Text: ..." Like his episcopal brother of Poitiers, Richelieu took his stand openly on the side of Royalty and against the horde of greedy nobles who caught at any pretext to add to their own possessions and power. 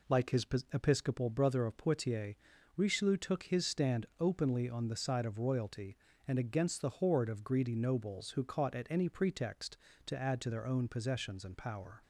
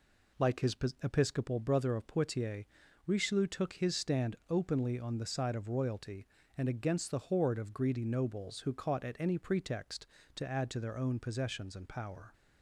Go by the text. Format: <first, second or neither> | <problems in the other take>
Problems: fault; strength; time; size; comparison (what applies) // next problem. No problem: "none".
neither | pauses between "his" and "episcopal"; slight; the same in both